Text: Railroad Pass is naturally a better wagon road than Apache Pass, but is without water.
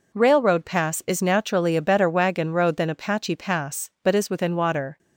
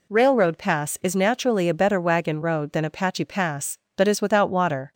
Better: second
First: says "within" for "without"; at 4.2 s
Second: none

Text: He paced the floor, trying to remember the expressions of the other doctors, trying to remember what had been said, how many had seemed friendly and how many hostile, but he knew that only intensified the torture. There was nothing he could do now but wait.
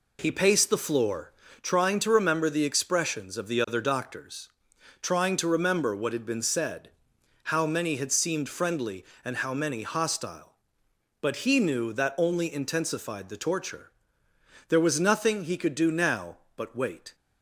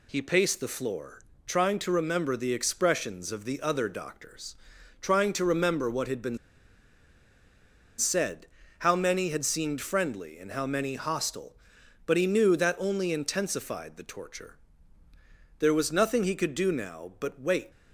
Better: first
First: none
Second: pauses between "been" and "said"; strong; at 6.3 s; 1.6 s long

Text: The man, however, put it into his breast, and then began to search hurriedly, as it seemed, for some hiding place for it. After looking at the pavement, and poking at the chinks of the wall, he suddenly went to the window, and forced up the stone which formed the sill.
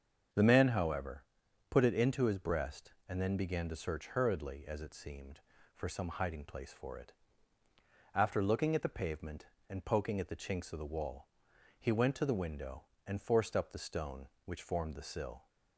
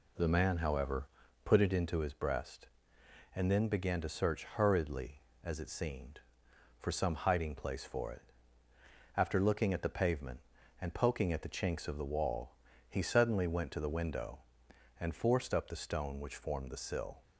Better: second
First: starts louder than the rest; until 1.7 s; 6.5 dB // skips "suddenly"; at 11.9 s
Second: none

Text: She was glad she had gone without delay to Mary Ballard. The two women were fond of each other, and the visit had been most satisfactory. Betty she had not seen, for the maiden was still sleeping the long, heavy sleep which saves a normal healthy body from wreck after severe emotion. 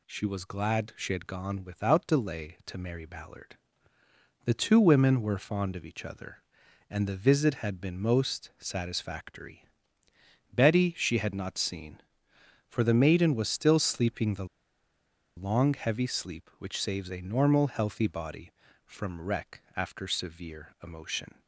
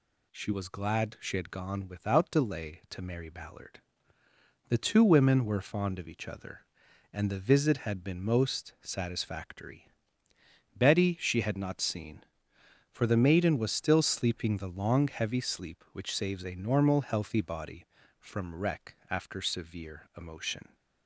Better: second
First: pauses between "the" and "long"; noticeable; at 14.4 s; 0.91 s long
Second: none

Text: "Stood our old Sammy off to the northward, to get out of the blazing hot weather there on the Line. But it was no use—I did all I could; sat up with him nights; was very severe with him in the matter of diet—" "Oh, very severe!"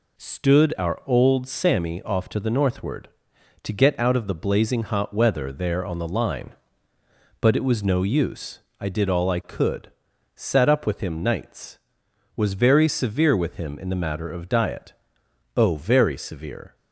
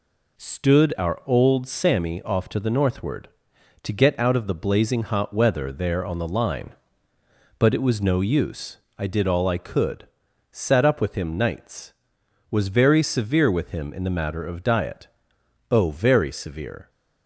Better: neither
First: none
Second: none

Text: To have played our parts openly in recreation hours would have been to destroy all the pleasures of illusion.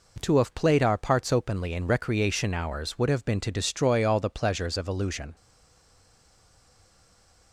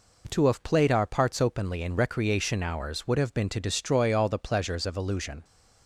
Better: second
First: stays silent after the last word; from 5.3 s on; 2.2 s long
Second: none

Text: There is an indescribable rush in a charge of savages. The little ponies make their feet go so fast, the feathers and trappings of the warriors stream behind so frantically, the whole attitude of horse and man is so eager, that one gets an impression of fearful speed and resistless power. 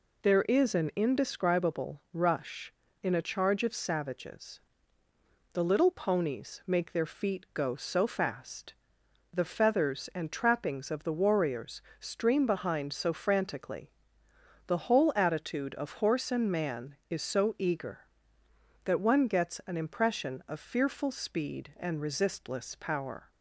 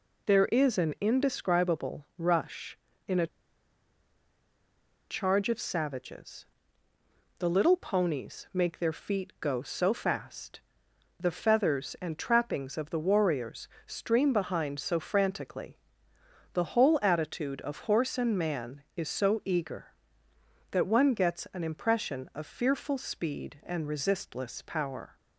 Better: first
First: pauses between "warriors" and "stream"; slight; at 11.8 s; 0.18 s long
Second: pauses between "a" and "charge"; strong; at 3.2 s; 1.8 s long // pauses between "warriors" and "stream"; slight; at 13.6 s; 0.18 s long

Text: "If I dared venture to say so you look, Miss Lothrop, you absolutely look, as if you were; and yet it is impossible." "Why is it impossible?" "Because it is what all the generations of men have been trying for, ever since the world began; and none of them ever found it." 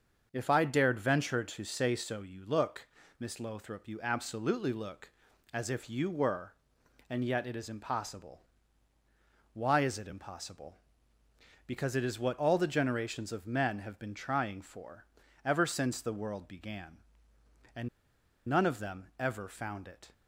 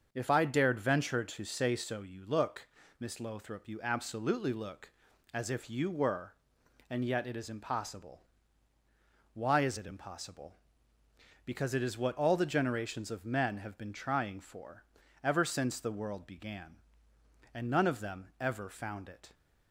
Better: second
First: starts louder than the rest; until 1.3 s; 6.5 dB // pauses between "and" and "none"; noticeable; at 17.8 s; 0.59 s long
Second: starts louder than the rest; until 1.1 s; 6.5 dB

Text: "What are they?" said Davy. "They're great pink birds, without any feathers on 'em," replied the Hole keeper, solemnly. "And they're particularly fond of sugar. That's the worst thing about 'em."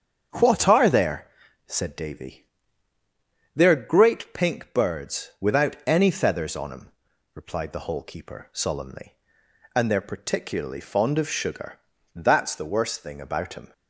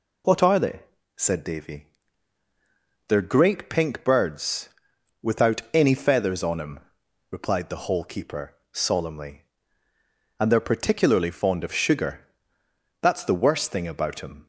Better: second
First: starts louder than the rest; strong; until 1.7 s; 7.5 dB // says "there" for "they"; at 0.9 s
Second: none

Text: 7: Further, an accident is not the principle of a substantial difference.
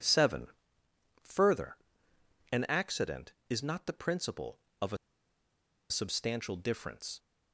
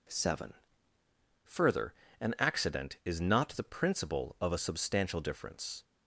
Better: second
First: pauses between "a" and "substantial"; noticeable; at 4.9 s; 0.93 s long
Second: none

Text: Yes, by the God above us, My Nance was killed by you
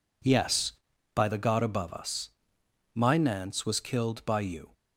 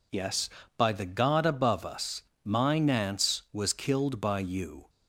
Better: neither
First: none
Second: none

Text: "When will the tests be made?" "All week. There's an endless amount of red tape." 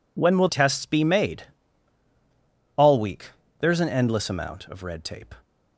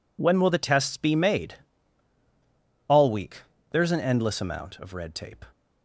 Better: second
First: skips "the"; at 0.4 s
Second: none

